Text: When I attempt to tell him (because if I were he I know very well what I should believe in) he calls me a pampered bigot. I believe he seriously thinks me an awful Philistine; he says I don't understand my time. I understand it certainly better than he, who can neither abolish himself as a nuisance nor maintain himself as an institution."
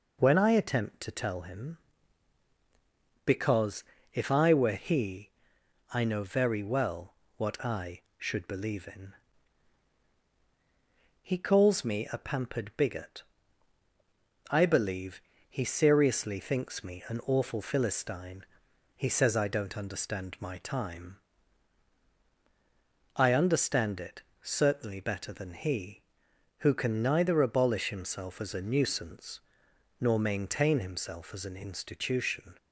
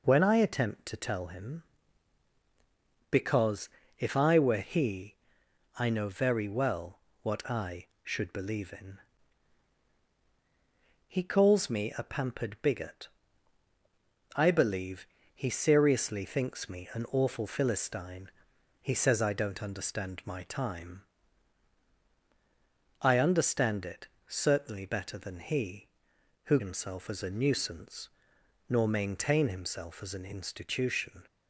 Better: first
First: pauses between "because" and "if"; slight; at 3.8 s; 0.30 s long // pauses between "he" and "I"; noticeable; at 5.2 s; 0.64 s long // pauses between "well" and "what"; slight; at 7.1 s; 0.24 s long // pauses between "believe" and "he"; slight; at 15.2 s; 0.26 s long // pauses between "it" and "certainly"; slight; at 24.2 s; 0.20 s long // pauses between "nuisance" and "nor"; noticeable; at 29.3 s; 0.62 s long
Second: pauses between "because" and "if"; slight; at 3.6 s; 0.30 s long // pauses between "he" and "I"; noticeable; at 5.1 s; 0.64 s long // pauses between "well" and "what"; slight; at 6.9 s; 0.24 s long // pauses between "believe" and "he"; slight; at 15.0 s; 0.26 s long // pauses between "it" and "certainly"; slight; at 24.0 s; 0.20 s long // skips "can neither abolish"; at 26.5 s // pauses between "nuisance" and "nor"; noticeable; at 28.0 s; 0.62 s long

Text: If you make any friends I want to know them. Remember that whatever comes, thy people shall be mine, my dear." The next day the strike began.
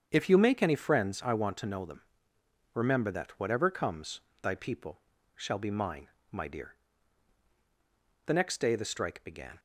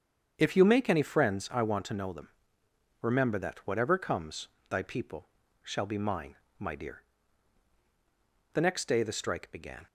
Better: neither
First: starts louder than the rest; strong; until 1.1 s; 7.5 dB // pauses between "people" and "shall"; slight; at 5.0 s; 0.34 s long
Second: starts louder than the rest; strong; until 1.3 s; 7.5 dB // pauses between "people" and "shall"; slight; at 5.2 s; 0.34 s long

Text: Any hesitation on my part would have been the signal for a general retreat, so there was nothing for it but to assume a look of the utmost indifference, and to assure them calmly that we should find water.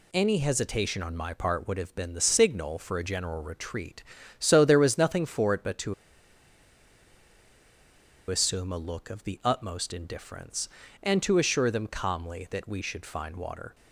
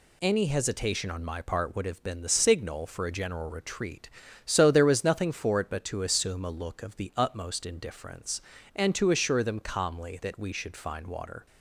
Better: second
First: pauses between "to" and "assume"; strong; at 5.9 s; 2.3 s long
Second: none

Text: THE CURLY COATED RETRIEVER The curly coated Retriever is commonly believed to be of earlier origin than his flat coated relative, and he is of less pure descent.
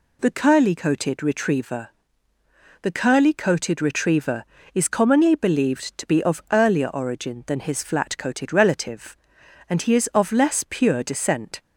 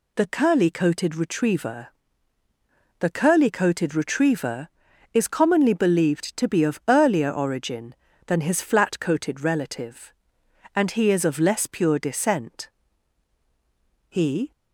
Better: first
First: pauses between "RETRIEVER" and "The"; noticeable; at 1.8 s; 0.94 s long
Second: pauses between "RETRIEVER" and "The"; at 1.8 s; 1.1 s long // goes on to say "He"; slight; from 14.0 s on; 0.42 s long

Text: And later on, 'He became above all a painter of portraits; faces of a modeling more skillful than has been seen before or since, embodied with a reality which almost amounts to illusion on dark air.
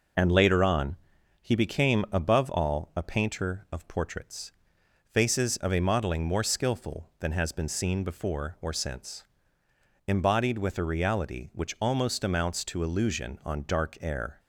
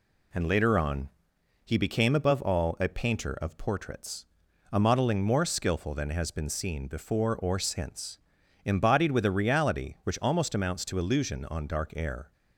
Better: first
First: none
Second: skips "faces of"; at 4.4 s

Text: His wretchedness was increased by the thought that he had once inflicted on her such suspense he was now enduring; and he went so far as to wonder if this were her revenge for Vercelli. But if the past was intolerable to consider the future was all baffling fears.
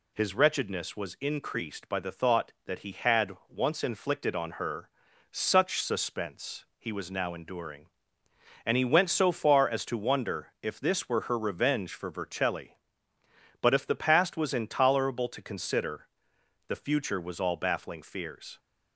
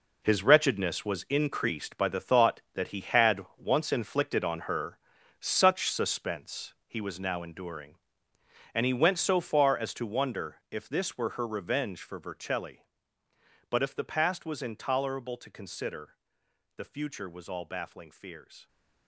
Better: first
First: pauses between "had" and "once"; slight; at 3.3 s; 0.16 s long // pauses between "her" and "such"; at 4.8 s; 0.42 s long // pauses between "consider" and "the"; noticeable; at 16.0 s; 0.62 s long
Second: gets quieter; strong; throughout; 11.5 dB // pauses between "had" and "once"; slight; at 3.4 s; 0.16 s long // pauses between "her" and "such"; at 4.9 s; 0.42 s long // pauses between "consider" and "the"; noticeable; at 16.1 s; 0.62 s long

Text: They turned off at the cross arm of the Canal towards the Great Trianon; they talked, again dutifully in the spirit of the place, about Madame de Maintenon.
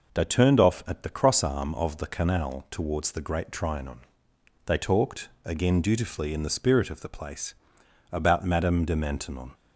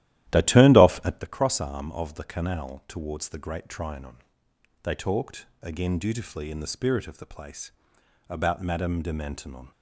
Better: first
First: none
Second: starts louder than the rest; strong; until 1.3 s; 14 dB

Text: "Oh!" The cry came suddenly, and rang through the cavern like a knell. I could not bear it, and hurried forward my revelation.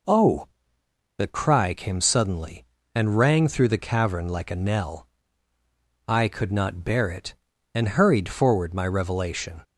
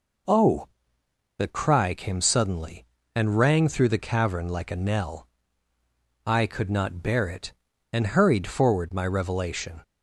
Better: neither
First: none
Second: none

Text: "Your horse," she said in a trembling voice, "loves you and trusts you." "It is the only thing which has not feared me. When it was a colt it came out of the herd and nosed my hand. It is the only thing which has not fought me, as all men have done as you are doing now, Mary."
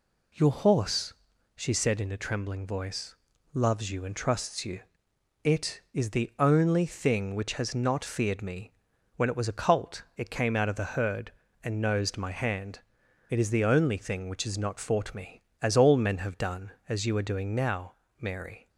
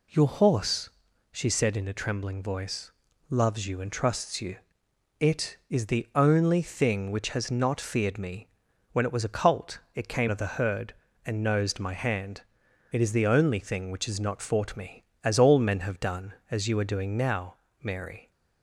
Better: first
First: none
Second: skips "out"; at 10.2 s

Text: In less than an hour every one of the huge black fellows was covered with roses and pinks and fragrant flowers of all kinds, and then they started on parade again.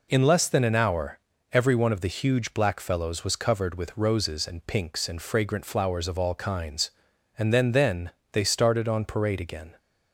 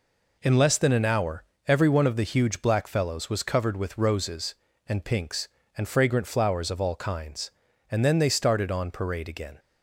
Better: second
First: pauses between "hour" and "every"; slight; at 1.1 s; 0.34 s long // says "then" twice; at 7.7 s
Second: pauses between "hour" and "every"; slight; at 1.4 s; 0.22 s long

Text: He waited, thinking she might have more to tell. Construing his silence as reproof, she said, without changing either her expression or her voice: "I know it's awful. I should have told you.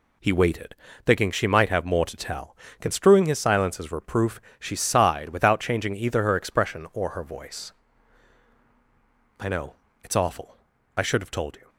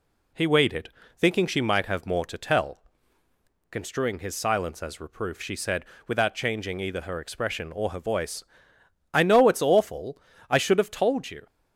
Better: second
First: says "sighed" for "said"; at 4.7 s // pauses between "know" and "it's"; slight; at 9.7 s; 0.28 s long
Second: none

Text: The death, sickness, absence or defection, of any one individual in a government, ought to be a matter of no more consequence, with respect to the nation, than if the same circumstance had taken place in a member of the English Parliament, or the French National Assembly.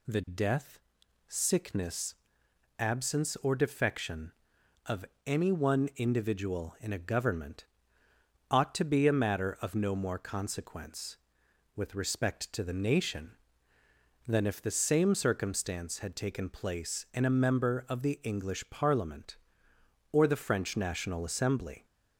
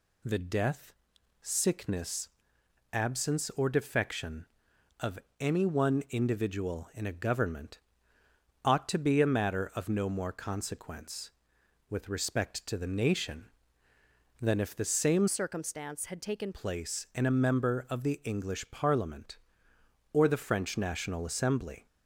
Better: first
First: pauses between "of" and "any"; slight; at 5.0 s; 0.22 s long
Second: pauses between "of" and "any"; slight; at 5.1 s; 0.22 s long // changes voice from "circumstance" to "taken"; from 15.2 to 16.5 s; 1.3 s long

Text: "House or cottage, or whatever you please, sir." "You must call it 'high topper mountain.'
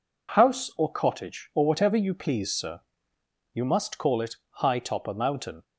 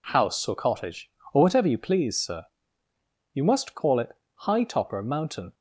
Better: neither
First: pauses between "it" and "high"; slight; at 4.3 s; 0.22 s long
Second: pauses between "it" and "high"; slight; at 4.1 s; 0.26 s long

